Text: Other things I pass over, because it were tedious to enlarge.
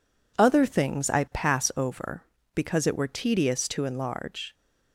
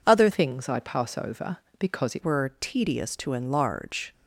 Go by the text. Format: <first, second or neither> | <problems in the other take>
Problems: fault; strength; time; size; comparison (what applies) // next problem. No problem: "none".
first | changes voice from "things" to "it"; from 0.3 to 2.2 s; 1.9 s long